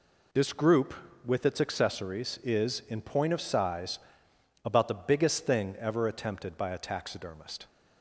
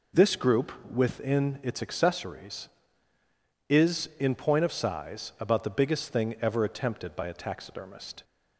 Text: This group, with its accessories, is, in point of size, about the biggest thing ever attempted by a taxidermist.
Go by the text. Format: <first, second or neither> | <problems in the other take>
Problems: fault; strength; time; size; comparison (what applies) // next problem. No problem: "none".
first | says "within" for "with"; at 0.9 s